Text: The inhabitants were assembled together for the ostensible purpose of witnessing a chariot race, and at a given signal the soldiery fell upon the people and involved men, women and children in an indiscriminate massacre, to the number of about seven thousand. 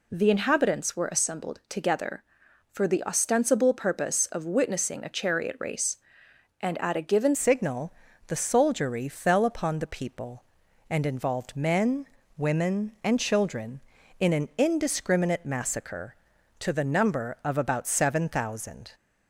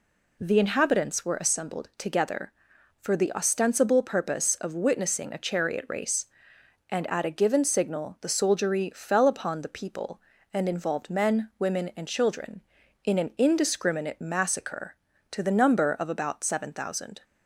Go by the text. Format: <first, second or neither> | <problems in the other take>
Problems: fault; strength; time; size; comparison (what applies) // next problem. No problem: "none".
second | changes voice at "signal"; from 7.3 s on; 11.6 s long // pauses between "signal" and "the"; slight; at 7.9 s; 0.34 s long